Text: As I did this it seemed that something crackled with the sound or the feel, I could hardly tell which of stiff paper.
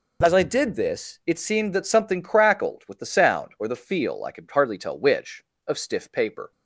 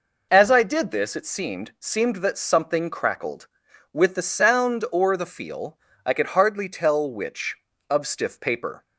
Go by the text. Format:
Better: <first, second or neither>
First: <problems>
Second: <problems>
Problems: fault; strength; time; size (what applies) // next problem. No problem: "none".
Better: first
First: none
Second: says "seemed" twice; at 1.7 s